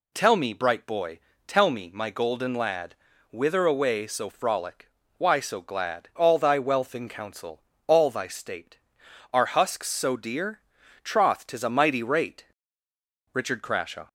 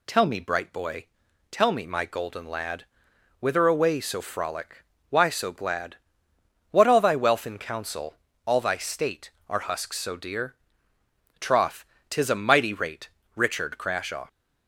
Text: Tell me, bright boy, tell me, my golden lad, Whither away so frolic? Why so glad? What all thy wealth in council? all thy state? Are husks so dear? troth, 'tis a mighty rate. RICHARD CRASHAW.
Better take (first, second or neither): second